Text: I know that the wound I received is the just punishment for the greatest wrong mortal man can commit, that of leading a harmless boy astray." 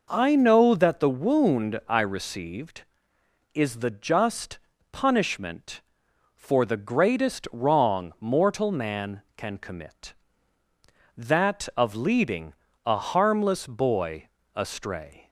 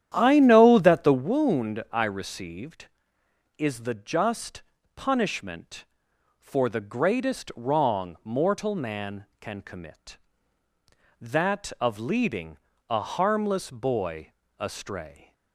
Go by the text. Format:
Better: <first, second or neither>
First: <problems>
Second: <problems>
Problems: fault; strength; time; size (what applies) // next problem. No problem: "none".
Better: first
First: pauses between "just" and "punishment"; slight; at 4.5 s; 0.34 s long // pauses between "leading" and "a"; slight; at 12.5 s; 0.34 s long // pauses between "boy" and "astray"; slight; at 14.2 s; 0.26 s long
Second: starts louder than the rest; strong; until 1.3 s; 10.5 dB // pauses between "just" and "punishment"; slight; at 4.6 s; 0.34 s long // pauses between "leading" and "a"; slight; at 12.5 s; 0.34 s long // pauses between "boy" and "astray"; slight; at 14.3 s; 0.26 s long